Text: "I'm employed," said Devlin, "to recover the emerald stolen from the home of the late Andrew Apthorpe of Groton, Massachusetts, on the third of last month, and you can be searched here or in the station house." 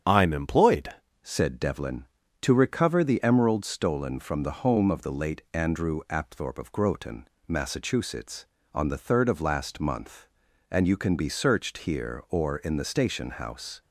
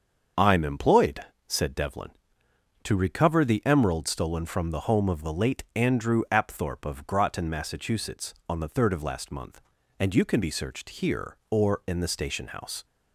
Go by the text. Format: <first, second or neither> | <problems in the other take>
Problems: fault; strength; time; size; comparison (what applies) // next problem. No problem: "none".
second | starts louder than the rest; strong; until 1.4 s; 8 dB; also in the second // changes voice at "said"; from 1.2 s on; 12.6 s long